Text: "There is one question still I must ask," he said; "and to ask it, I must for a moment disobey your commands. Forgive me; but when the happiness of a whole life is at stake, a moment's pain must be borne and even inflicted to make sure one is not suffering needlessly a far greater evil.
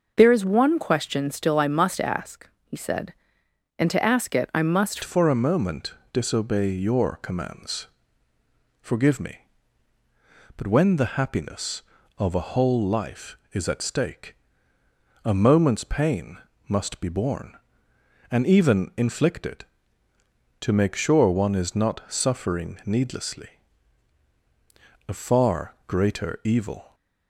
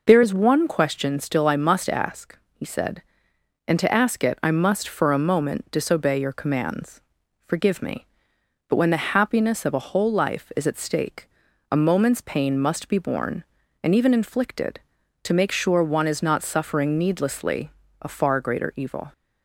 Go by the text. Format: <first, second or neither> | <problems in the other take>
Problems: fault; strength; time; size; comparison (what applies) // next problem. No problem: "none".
second | changes voice at "for"; from 5.0 s on; 21.9 s long // pauses between "moment" and "disobey"; slight; at 5.9 s; 0.18 s long // pauses between "pain" and "must"; slight; at 16.3 s; 0.32 s long // pauses between "needlessly" and "a"; strong; at 23.4 s; 1.6 s long; slight in the second